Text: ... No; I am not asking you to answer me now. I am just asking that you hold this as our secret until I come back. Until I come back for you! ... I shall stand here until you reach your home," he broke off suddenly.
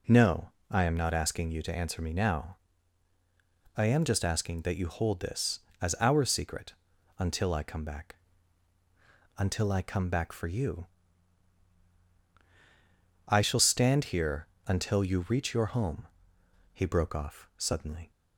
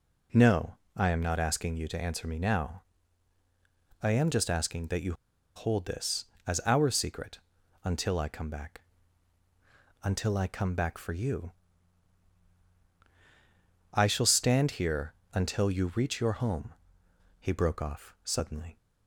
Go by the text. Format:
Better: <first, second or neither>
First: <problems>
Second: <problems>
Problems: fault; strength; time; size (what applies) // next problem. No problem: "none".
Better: first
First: pauses between "secret" and "until"; at 6.7 s; 0.44 s long // pauses between "here" and "until"; slight; at 14.4 s; 0.20 s long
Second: pauses between "you" and "hold"; at 5.1 s; 0.42 s long // pauses between "secret" and "until"; at 7.3 s; 0.44 s long // pauses between "here" and "until"; slight; at 15.1 s; 0.20 s long